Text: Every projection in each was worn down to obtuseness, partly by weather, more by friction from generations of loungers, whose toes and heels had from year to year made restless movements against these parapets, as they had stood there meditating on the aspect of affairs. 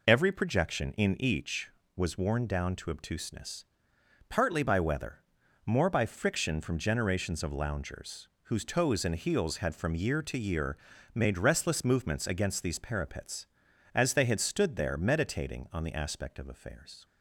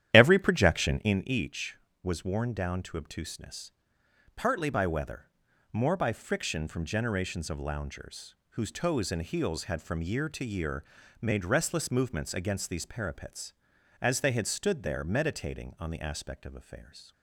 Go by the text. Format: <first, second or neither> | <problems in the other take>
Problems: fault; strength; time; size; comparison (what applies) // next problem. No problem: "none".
first | starts louder than the rest; strong; until 1.2 s; 11 dB // pauses between "year" and "made"; at 10.8 s; 0.38 s long; also in the first